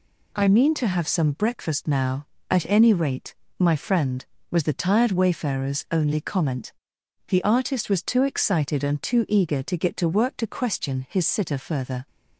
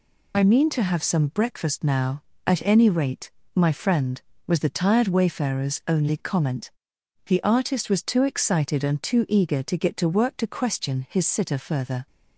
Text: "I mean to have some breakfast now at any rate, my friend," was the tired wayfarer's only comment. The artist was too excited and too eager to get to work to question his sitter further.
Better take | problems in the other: first | loses the start of "I"; at 0.3 s; 45 ms

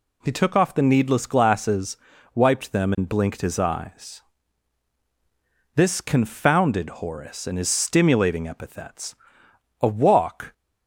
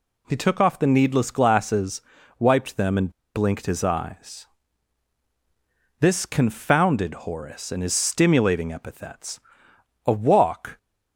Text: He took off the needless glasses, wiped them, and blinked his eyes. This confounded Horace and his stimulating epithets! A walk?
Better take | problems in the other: first | pauses between "and" and "blinked"; slight; at 3.1 s; 0.24 s long

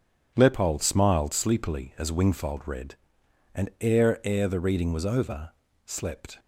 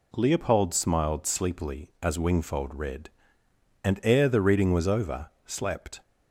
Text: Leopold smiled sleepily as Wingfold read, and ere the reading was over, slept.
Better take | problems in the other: second | says "ere" twice; at 4.2 s

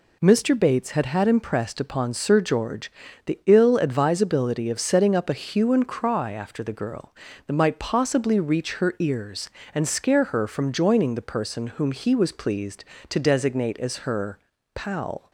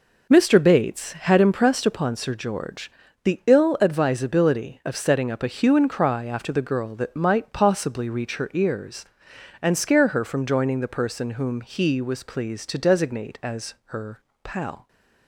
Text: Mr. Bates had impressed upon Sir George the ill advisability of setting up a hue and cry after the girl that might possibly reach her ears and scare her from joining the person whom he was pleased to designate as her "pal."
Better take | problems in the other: second | says "had" twice; at 1.0 s // pauses between "George" and "the"; slight; at 2.9 s; 0.36 s long; slight in the second // pauses between "her" and "pal"; slight; at 14.4 s; 0.34 s long; slight in the second

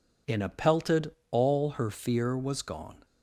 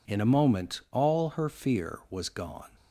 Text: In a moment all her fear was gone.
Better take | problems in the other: second | says "pelted" for "moment"; at 0.4 s

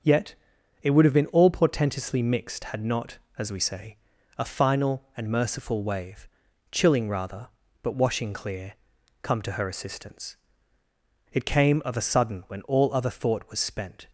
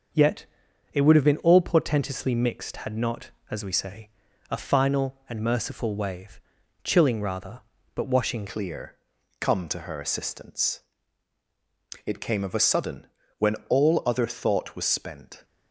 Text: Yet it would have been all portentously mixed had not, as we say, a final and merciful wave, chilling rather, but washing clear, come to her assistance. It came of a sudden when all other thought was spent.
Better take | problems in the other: first | starts louder than the rest; until 1.6 s; 6.5 dB; also in the first // pauses between "Yet" and "it"; noticeable; at 0.4 s; 0.48 s long; noticeable in the first // changes voice at "clear"; from 8.4 s on; 7.0 s long // pauses between "sudden" and "when"; slight; at 13.0 s; 0.30 s long

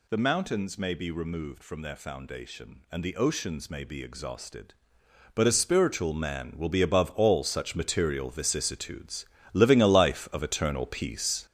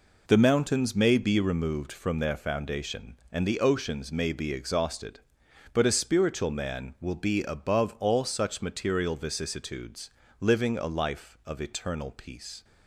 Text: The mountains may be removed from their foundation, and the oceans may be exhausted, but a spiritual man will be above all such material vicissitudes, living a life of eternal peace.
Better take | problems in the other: second | gets louder; strong; throughout; 7.5 dB

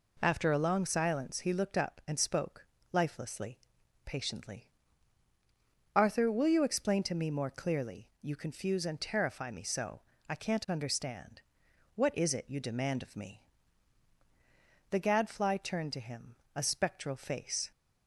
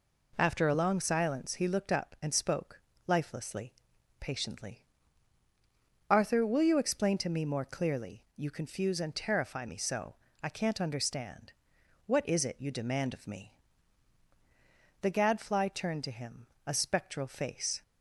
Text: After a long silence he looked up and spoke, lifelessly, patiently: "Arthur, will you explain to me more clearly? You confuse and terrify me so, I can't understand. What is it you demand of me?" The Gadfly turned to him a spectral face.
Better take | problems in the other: neither | pauses between "him" and "a"; slight; the same in both

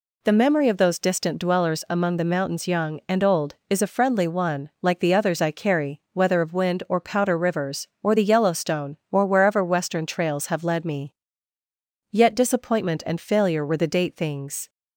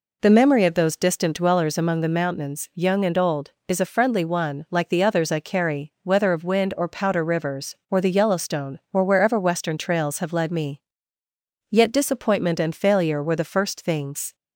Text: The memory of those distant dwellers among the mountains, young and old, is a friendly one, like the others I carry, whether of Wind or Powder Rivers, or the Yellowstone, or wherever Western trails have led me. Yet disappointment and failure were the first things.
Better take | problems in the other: second | says "date" for "first"; at 13.8 s

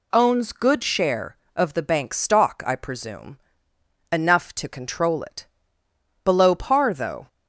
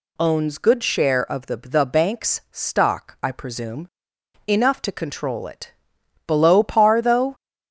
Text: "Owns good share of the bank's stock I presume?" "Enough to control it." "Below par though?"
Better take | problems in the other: first | says "the" twice; at 1.5 s

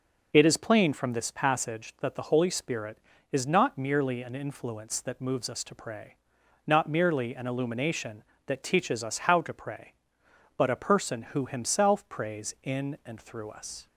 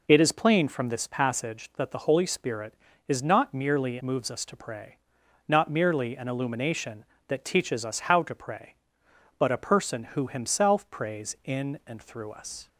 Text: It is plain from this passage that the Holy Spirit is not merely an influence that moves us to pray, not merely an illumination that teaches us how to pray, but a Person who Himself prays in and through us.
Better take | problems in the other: first | skips "an influence that"; at 4.0 s

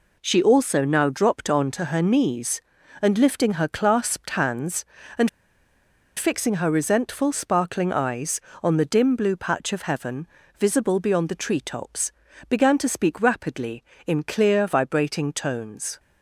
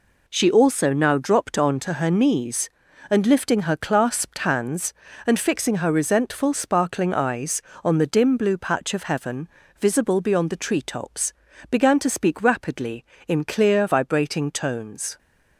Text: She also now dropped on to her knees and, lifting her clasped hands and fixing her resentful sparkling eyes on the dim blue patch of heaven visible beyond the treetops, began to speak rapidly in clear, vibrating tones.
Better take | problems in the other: second | pauses between "and" and "fixing"; noticeable; at 5.2 s; 0.87 s long // pauses between "heaven" and "visible"; slight; at 10.2 s; 0.32 s long; slight in the second

